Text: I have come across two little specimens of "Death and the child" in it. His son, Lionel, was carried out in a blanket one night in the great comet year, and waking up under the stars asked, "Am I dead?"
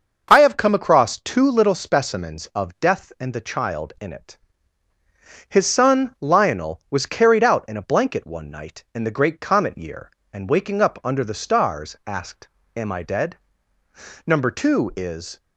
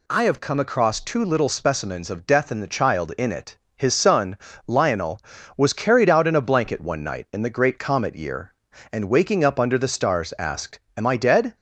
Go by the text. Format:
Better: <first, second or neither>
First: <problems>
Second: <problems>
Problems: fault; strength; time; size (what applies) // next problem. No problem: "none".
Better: second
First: goes on to say "Number two is"; noticeable; from 14.2 s on; 1.1 s long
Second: none